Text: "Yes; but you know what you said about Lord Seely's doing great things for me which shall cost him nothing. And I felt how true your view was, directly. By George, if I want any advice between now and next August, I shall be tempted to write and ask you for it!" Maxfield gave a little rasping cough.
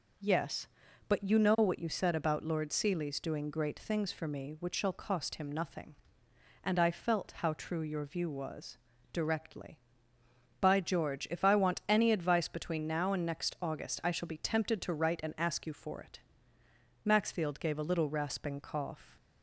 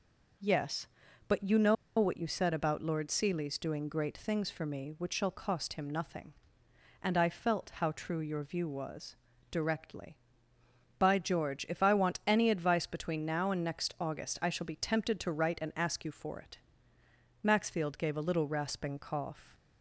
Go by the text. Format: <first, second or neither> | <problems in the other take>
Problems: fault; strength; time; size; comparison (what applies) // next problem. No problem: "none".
first | pauses between "know" and "what"; slight; at 1.7 s; 0.23 s long